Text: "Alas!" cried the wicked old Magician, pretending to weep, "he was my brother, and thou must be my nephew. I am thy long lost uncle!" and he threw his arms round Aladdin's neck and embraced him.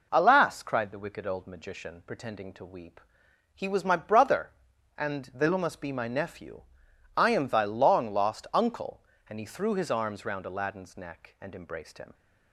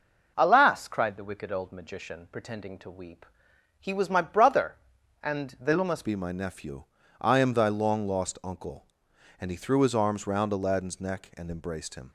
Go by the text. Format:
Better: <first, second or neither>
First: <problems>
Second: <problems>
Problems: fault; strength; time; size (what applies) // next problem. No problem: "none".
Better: first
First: none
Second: changes voice at "be"; from 6.0 s on; 6.1 s long